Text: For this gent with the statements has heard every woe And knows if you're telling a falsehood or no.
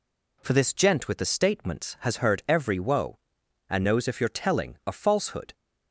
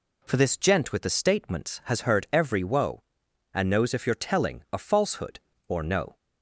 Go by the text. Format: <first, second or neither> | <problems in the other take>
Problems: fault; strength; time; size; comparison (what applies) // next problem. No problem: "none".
second | stops before "or no"; at 5.5 s